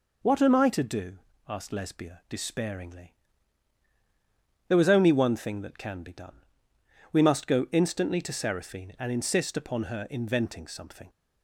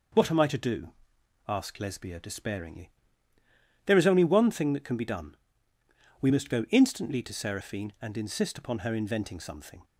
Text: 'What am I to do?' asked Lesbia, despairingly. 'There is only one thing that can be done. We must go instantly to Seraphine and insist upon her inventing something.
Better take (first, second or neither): second